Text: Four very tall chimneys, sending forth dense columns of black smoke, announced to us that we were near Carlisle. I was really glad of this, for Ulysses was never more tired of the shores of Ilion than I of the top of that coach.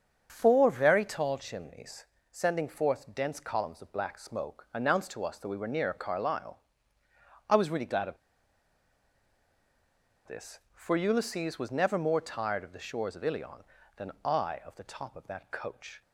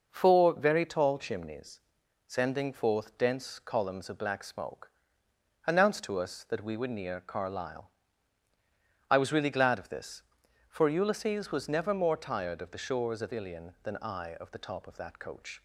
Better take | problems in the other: second | starts louder than the rest; strong; until 1.3 s; 7.5 dB // pauses between "of" and "this"; strong; at 8.1 s; 2.0 s long

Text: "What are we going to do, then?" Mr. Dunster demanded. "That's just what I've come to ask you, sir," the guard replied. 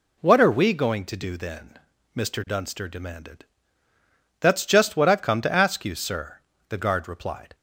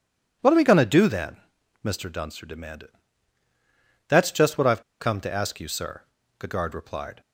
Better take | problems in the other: first | pauses between "I've" and "come"; slight; at 4.8 s; 0.17 s long

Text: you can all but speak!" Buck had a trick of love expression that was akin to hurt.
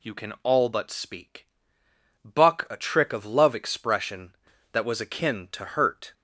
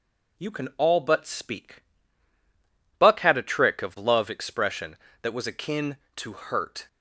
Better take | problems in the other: second | skips "had"; at 2.6 s

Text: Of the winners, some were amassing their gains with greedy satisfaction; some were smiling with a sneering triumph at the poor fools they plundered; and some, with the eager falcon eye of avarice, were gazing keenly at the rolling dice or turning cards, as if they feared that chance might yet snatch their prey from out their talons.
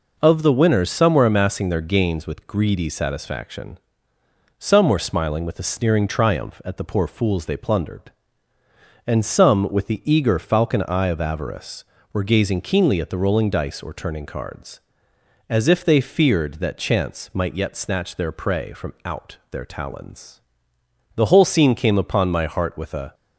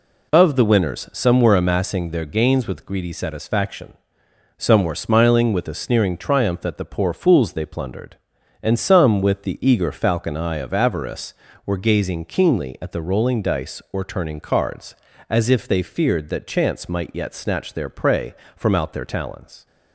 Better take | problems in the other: second | goes on to say "The whole scene came upon my heart with a"; strong; from 21.1 s on; 2.0 s long

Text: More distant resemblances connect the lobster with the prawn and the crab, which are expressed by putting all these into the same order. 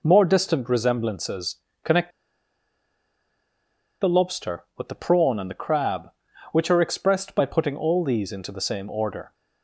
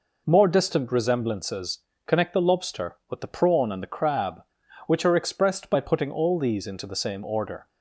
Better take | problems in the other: second | pauses between "resemblances" and "connect"; slight; at 1.5 s; 0.26 s long; slight in the second // pauses between "connect" and "the"; strong; at 2.0 s; 1.9 s long

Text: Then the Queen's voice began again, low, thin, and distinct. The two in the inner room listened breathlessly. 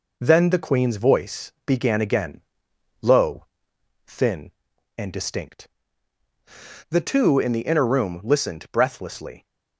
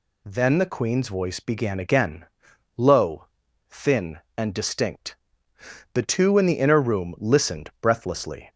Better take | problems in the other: second | gets quieter; noticeable; throughout; 4 dB

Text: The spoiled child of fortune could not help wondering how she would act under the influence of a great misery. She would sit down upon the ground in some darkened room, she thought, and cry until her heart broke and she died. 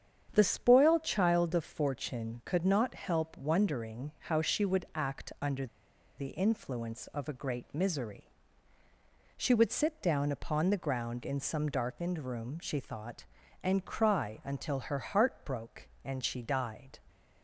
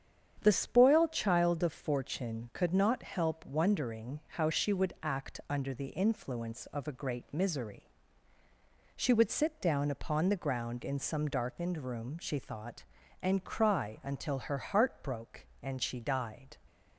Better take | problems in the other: second | starts louder than the rest; strong; until 1.3 s; 8 dB; strong in the second // pauses between "under" and "the"; noticeable; at 5.6 s; 0.51 s long

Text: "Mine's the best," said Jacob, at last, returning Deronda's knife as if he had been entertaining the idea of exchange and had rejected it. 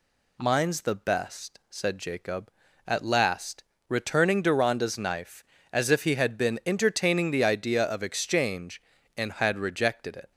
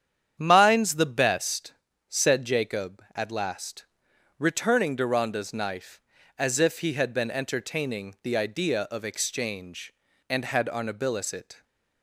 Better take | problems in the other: first | starts louder than the rest; strong; until 1.4 s; 9 dB // says "arnabilis" for "rejected"; at 10.6 s

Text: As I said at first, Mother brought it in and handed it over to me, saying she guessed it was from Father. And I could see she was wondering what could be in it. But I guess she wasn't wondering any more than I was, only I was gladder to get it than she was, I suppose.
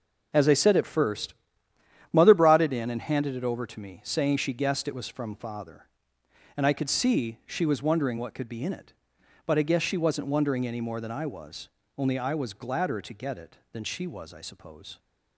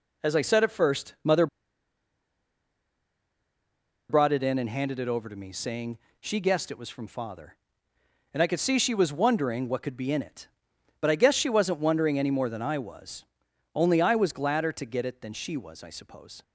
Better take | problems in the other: first | pauses between "Mother" and "brought"; strong; at 1.4 s; 2.6 s long // pauses between "saying" and "she"; slight; at 5.9 s; 0.20 s long

